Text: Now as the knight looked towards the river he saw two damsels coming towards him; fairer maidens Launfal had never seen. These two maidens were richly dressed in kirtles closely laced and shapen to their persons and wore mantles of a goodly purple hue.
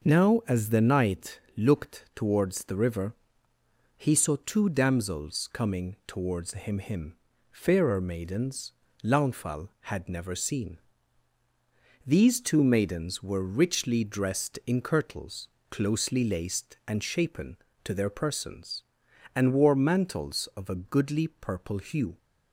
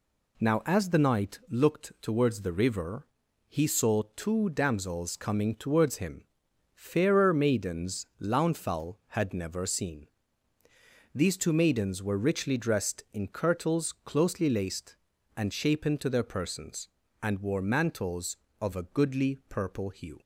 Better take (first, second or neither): second